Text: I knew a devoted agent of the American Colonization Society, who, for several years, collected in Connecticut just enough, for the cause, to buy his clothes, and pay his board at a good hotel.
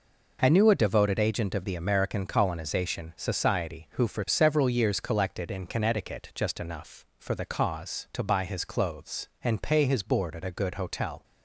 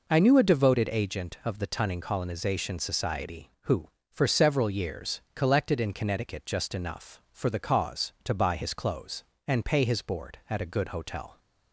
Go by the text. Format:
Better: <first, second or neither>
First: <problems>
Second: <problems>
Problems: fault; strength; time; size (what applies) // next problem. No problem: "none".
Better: first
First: none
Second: says "Tunning" for "American"; at 1.6 s